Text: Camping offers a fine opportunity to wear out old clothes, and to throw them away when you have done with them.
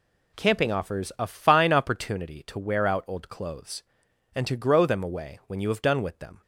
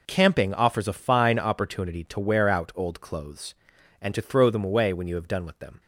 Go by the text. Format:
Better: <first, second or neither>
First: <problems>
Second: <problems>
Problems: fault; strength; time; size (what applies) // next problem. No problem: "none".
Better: second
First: says "grow" for "throw"; at 4.5 s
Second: none